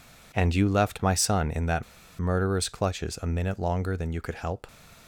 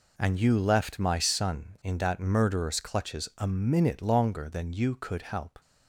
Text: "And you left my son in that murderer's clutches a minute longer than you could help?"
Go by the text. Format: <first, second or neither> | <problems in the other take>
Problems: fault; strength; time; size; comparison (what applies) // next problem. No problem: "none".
second | pauses between "that" and "murderer's"; slight; at 1.8 s; 0.35 s long